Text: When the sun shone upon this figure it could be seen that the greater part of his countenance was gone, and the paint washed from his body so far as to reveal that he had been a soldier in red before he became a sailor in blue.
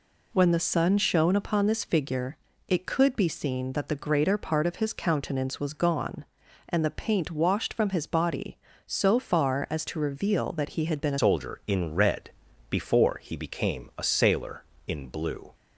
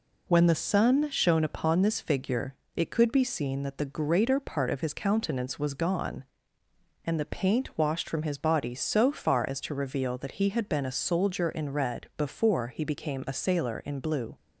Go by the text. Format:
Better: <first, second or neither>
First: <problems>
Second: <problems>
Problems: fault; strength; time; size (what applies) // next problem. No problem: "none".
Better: second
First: pauses between "figure" and "it"; slight; at 2.3 s; 0.28 s long // changes voice at "soldier"; from 11.1 s on; 4.4 s long // pauses between "red" and "before"; slight; at 12.3 s; 0.36 s long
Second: pauses between "figure" and "it"; slight; at 2.5 s; 0.22 s long